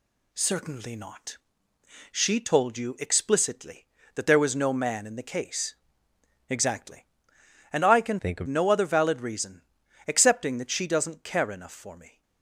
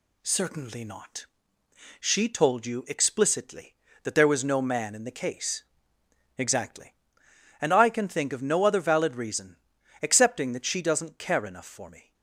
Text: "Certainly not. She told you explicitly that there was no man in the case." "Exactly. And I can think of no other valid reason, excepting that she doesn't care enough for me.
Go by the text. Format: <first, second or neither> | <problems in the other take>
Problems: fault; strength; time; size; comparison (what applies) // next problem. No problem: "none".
second | changes voice from "think" to "of"; from 8.1 to 8.4 s; 0.3 s long